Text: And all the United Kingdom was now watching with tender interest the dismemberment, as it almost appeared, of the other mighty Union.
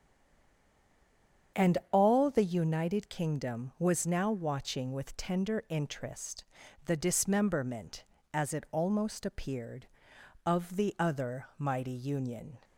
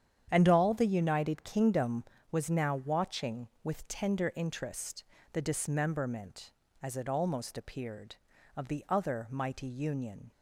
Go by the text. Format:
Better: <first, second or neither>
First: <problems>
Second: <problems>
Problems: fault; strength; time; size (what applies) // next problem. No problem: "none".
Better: second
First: stays silent before the first word; noticeable; until 1.5 s; 1.5 s long // starts louder than the rest; strong; until 2.7 s; 8 dB // pauses between "interest" and "the"; at 6.4 s; 0.42 s long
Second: starts louder than the rest; strong; until 1.3 s; 9 dB // pauses between "interest" and "the"; slight; at 5.0 s; 0.30 s long